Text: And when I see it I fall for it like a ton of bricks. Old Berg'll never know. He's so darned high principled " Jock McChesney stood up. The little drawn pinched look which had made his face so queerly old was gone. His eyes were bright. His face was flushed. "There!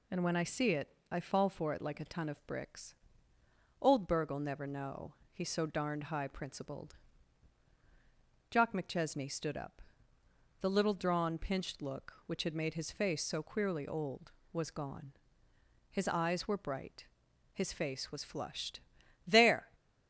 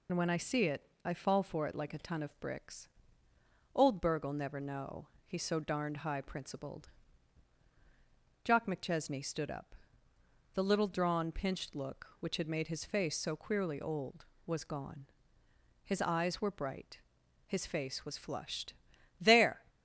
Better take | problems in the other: first | loses the start of "And"; at 0.0 s; 55 ms // pauses between "it" and "I"; slight; at 0.8 s; 0.22 s long; slight in the first

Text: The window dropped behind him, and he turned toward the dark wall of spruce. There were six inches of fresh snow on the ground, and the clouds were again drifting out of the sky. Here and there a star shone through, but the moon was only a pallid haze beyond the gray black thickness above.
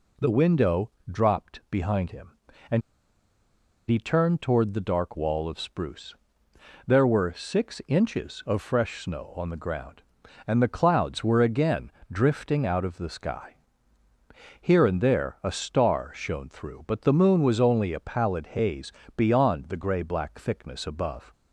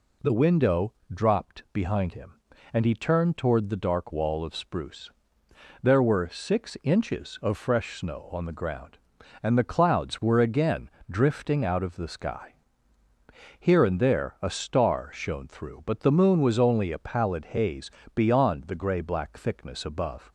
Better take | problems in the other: second | pauses between "window" and "dropped"; slight; at 0.9 s; 0.18 s long; slight in the second // pauses between "and" and "he"; at 2.8 s; 1.0 s long // pauses between "again" and "drifting"; slight; at 11.9 s; 0.18 s long; slight in the second // pauses between "haze" and "beyond"; slight; at 18.9 s; 0.24 s long; slight in the second

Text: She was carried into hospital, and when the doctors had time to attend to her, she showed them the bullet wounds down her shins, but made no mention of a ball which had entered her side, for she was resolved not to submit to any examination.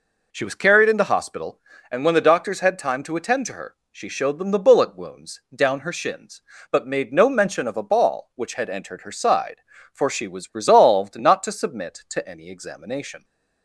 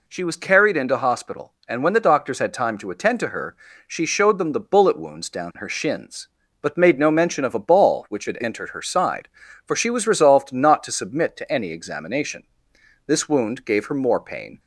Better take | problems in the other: first | goes on to say "This wound gave her more pain"; from 13.0 s on; 1.5 s long

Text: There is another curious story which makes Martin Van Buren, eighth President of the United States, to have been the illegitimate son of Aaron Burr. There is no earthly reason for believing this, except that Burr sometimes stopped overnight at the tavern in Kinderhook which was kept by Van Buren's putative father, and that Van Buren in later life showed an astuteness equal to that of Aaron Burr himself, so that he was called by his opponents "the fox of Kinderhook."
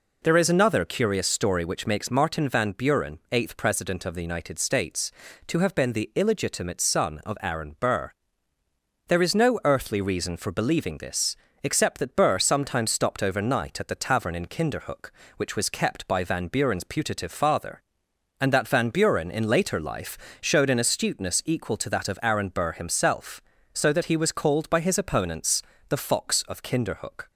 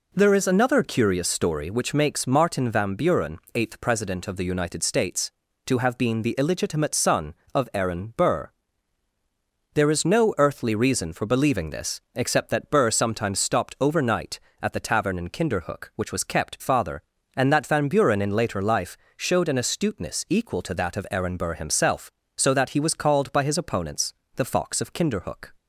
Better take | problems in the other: first | skips "by Van Buren's putative"; at 16.6 s // pauses between "life" and "showed"; slight; at 18.9 s; 0.20 s long; slight in the first // pauses between "opponents" and "the"; slight; at 24.1 s; 0.22 s long; slight in the first

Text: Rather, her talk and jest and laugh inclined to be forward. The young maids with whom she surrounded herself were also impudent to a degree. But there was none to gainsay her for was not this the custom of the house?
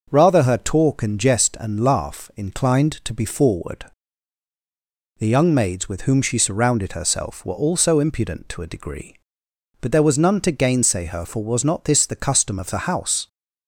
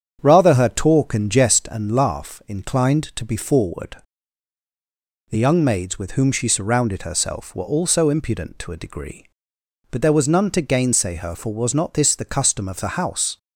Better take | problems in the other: first | starts louder than the rest; strong; until 1.9 s; 7.5 dB

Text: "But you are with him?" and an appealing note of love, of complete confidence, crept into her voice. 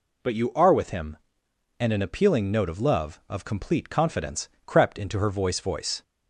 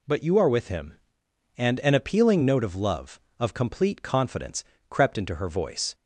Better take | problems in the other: second | says "voice" twice; at 5.6 s

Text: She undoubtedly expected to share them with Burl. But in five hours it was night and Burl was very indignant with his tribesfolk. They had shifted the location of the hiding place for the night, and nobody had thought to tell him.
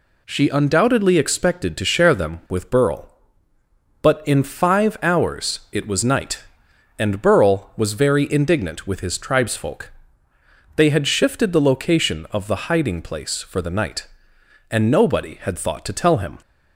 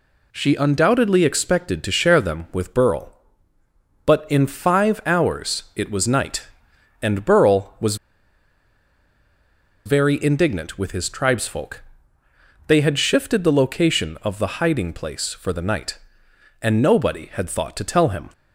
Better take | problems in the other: first | pauses between "was" and "very"; strong; at 7.9 s; 1.9 s long

